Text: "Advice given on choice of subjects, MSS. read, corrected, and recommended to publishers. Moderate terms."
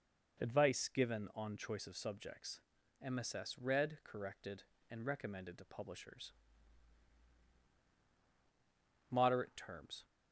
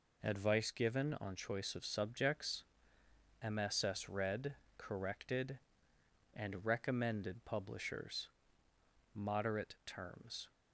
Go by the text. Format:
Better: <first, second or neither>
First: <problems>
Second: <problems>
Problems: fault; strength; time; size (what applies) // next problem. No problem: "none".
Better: first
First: none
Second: skips "to"; at 7.4 s